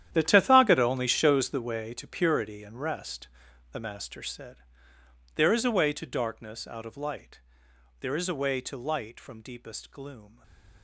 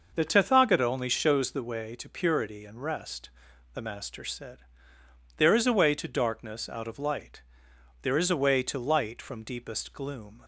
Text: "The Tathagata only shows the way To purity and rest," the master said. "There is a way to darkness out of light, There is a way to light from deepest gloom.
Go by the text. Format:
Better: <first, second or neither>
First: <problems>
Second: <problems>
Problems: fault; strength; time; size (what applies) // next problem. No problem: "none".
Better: second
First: gets quieter; strong; throughout; 15 dB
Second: none